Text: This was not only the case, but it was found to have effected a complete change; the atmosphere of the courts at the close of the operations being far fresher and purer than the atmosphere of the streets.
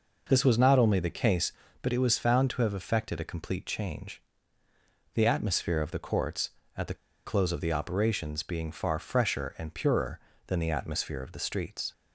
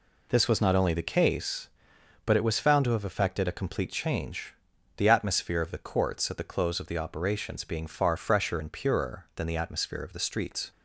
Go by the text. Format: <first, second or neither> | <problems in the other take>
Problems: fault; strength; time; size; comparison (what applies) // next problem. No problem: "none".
second | pauses between "the" and "close"; slight; at 6.9 s; 0.30 s long